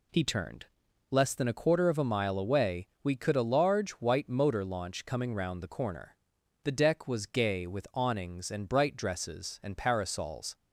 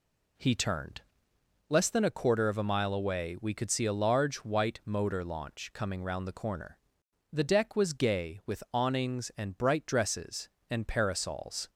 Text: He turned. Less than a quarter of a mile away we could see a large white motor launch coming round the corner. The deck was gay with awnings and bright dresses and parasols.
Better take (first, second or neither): second